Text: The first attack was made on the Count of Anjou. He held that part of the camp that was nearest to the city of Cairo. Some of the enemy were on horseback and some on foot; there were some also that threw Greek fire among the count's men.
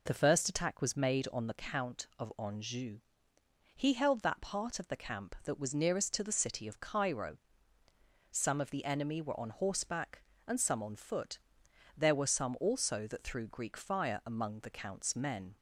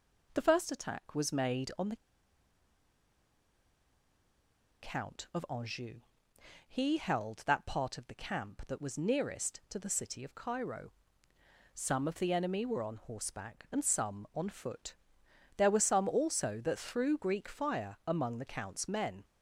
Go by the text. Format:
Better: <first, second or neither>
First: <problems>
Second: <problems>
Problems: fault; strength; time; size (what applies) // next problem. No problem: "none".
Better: first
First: none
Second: pauses between "the" and "Count"; strong; at 1.9 s; 2.8 s long